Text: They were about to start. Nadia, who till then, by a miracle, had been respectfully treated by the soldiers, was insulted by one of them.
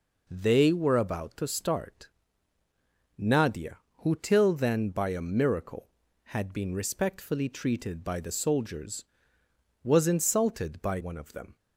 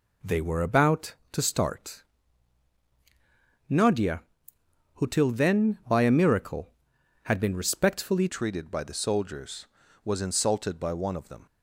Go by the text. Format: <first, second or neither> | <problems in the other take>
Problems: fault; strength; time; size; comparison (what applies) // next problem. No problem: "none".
first | changes voice at "treated"; from 8.2 s on; 3.2 s long